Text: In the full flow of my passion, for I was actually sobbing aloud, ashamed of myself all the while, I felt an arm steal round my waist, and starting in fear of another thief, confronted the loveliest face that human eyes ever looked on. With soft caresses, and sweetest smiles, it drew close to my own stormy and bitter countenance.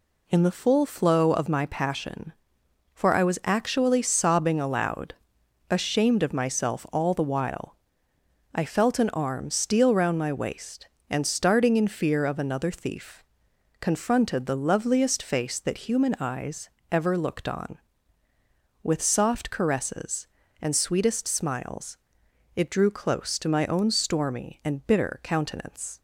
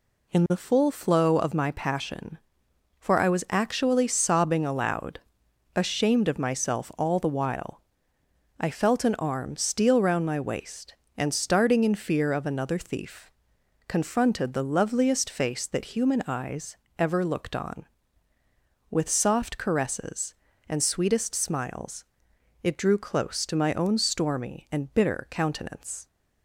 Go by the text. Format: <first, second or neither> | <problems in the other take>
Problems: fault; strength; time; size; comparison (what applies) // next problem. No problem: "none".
neither | pauses between "eyes" and "ever"; slight; the same in both